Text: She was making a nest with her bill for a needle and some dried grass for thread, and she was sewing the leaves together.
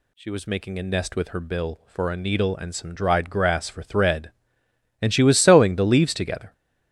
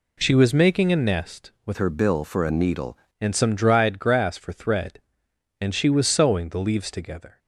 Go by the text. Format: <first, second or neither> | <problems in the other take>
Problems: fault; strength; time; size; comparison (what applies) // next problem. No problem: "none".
first | changes voice from "her" to "needle"; from 1.7 to 2.9 s; 1.2 s long